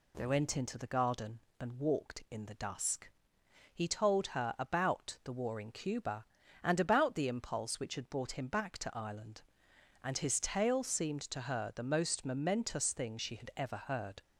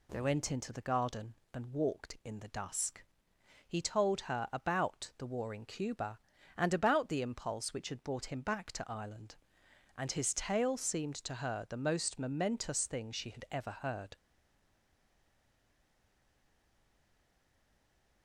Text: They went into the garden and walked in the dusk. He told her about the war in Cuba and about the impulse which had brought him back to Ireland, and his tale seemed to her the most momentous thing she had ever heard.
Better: first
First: none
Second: stays silent after the last word; strong; from 14.1 s on; 4.1 s long

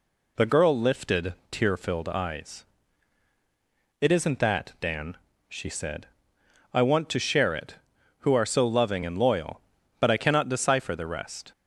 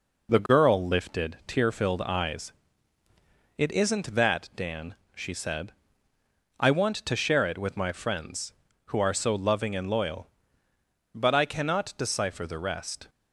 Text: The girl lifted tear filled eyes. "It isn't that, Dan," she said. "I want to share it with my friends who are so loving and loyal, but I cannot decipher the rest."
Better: second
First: pauses between "lifted" and "tear"; slight; at 1.3 s; 0.18 s long // skips "with my friends"; at 7.9 s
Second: none

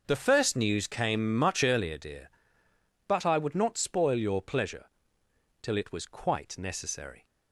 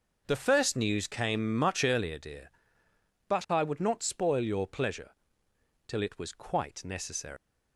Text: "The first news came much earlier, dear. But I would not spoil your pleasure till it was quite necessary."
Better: first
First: pauses between "pleasure" and "till"; noticeable; at 4.8 s; 0.76 s long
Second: pauses between "pleasure" and "till"; noticeable; at 5.1 s; 0.76 s long // leaves "necessary" unfinished; at 7.3 s; 145 ms

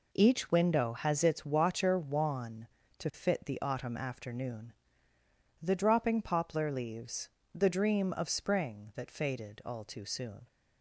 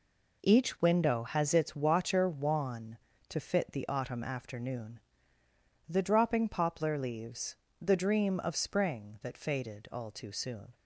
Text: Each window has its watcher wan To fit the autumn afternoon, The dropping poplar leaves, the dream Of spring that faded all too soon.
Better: neither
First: none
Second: none

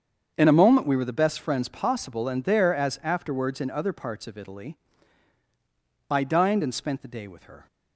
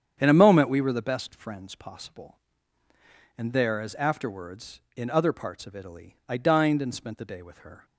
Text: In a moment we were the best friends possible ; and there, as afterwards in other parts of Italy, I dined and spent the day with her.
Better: neither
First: starts louder than the rest; strong; until 1.3 s; 7.5 dB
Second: starts louder than the rest; strong; until 1.2 s; 8.5 dB

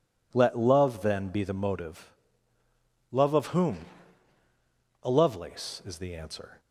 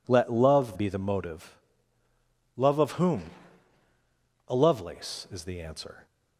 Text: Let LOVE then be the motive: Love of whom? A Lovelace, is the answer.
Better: first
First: none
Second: skips "then"; at 0.7 s

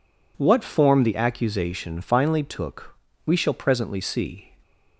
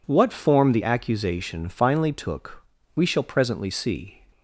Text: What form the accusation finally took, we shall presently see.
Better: neither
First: none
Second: none

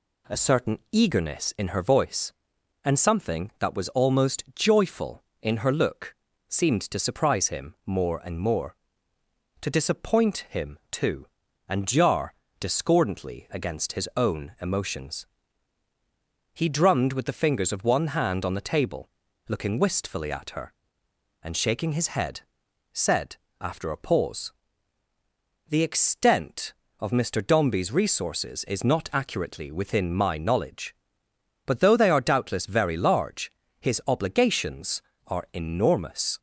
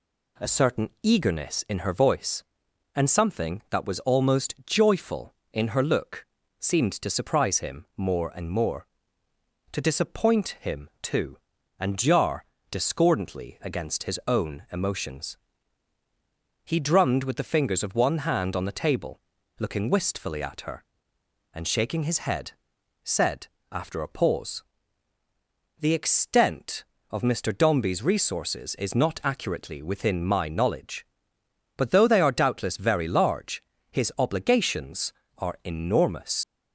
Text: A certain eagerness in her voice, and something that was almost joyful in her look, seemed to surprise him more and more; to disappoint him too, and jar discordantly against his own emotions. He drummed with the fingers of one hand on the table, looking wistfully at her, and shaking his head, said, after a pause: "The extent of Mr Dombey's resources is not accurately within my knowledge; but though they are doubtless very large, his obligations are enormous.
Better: first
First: pauses between "jar" and "discordantly"; slight; at 12.3 s; 0.26 s long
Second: pauses between "jar" and "discordantly"; slight; at 12.4 s; 0.26 s long // leaves "enormous" unfinished; at 36.4 s; 60 ms

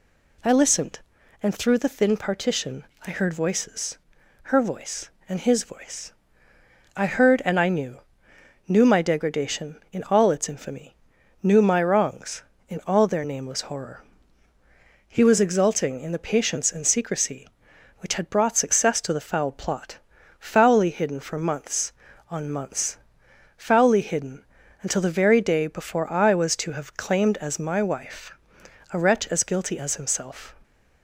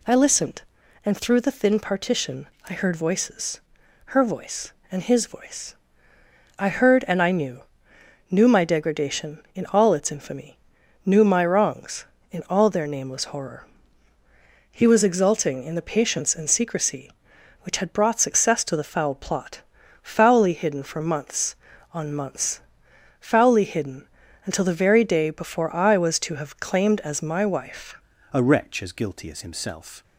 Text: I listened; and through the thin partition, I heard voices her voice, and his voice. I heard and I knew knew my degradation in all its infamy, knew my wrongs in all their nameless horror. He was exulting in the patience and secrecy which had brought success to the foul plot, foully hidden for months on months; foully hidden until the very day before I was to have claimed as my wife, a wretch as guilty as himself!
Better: first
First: pauses between "voices" and "her"; noticeable; at 3.9 s; 0.46 s long // pauses between "knew" and "knew"; noticeable; at 7.9 s; 0.66 s long // pauses between "hidden" and "until"; at 24.4 s; 0.38 s long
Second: pauses between "voices" and "her"; noticeable; at 3.5 s; 0.46 s long // pauses between "knew" and "knew"; noticeable; at 7.6 s; 0.66 s long // pauses between "hidden" and "until"; at 24.0 s; 0.38 s long // changes voice at "a"; from 28.3 s on; 1.7 s long

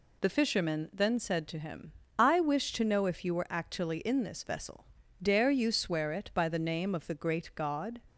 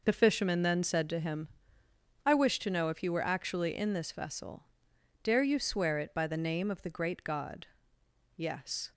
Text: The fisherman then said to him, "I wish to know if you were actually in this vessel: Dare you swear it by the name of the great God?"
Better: first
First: none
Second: goes on to say "Yes"; from 8.3 s on; 0.56 s long

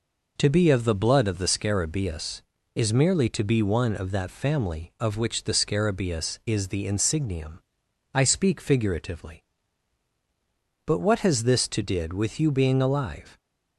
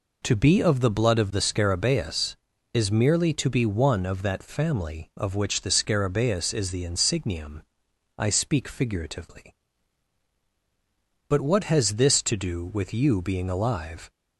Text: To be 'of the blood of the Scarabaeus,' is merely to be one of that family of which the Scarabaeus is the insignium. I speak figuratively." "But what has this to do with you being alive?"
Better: second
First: says "did" for "do"; at 11.8 s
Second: none

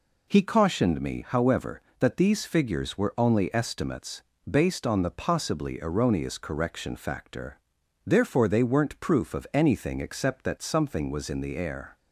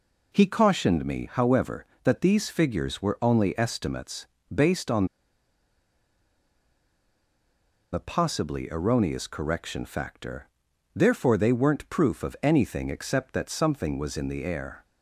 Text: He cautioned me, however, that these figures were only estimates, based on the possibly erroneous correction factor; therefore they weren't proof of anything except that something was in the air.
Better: first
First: none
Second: pauses between "on" and "the"; strong; at 5.0 s; 2.8 s long

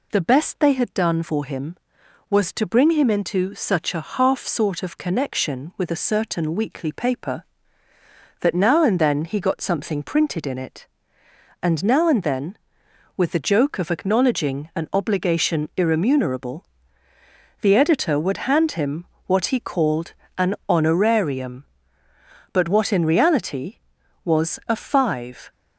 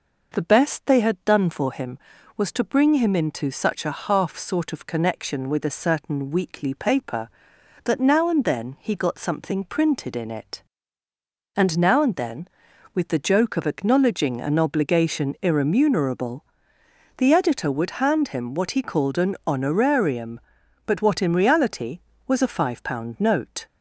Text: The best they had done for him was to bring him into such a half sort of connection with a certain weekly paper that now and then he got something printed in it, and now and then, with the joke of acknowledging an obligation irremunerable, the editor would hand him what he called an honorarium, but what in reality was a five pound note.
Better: second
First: pauses between "him" and "what"; slight; at 19.0 s; 0.20 s long // pauses between "called" and "an"; slight; at 20.1 s; 0.24 s long // stops before "pound note"; at 25.5 s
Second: none

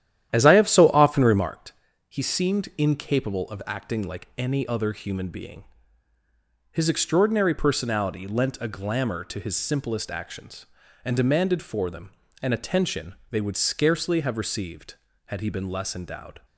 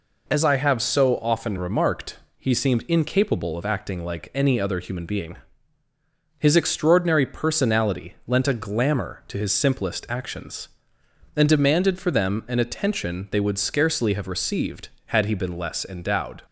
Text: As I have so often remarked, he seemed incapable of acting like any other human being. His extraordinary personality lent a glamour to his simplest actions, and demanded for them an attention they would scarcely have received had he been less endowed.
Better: second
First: starts louder than the rest; strong; until 1.5 s; 11 dB // pauses between "them" and "an"; slight; at 12.1 s; 0.32 s long // pauses between "attention" and "they"; slight; at 13.1 s; 0.16 s long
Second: none

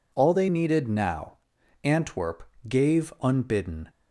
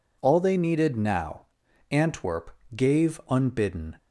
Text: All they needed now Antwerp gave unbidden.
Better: neither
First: pauses between "now" and "Antwerp"; noticeable; at 1.3 s; 0.46 s long // pauses between "Antwerp" and "gave"; slight; at 2.4 s; 0.26 s long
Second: pauses between "now" and "Antwerp"; at 1.4 s; 0.44 s long // pauses between "Antwerp" and "gave"; slight; at 2.4 s; 0.26 s long

